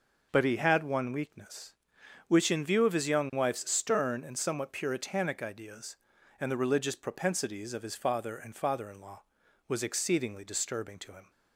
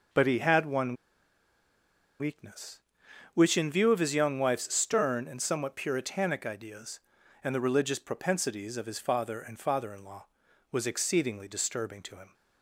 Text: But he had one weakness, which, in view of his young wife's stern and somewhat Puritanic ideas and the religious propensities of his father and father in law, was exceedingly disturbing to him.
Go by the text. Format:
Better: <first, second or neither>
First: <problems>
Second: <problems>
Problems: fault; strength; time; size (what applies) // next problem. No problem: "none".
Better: first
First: none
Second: pauses between "one" and "weakness"; strong; at 0.9 s; 1.2 s long